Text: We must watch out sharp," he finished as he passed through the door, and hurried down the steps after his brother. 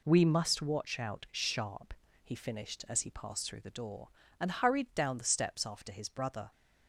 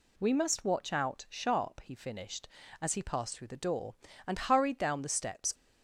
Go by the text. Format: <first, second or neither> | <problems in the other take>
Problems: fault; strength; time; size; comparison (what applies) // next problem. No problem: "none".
first | stops before "after his brother"; at 5.5 s